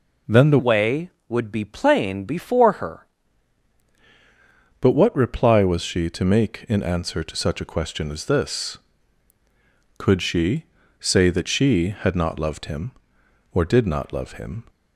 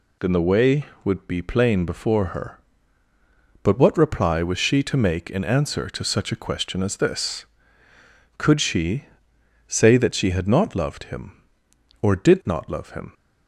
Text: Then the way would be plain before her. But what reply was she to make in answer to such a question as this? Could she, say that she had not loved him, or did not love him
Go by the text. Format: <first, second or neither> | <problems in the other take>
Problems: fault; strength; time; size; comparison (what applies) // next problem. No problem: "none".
second | changes voice from "way" to "her"; from 0.5 to 3.0 s; 2.5 s long